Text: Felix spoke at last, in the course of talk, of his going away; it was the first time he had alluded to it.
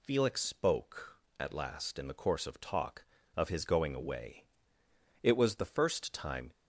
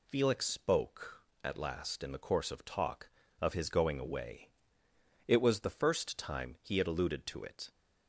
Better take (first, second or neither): second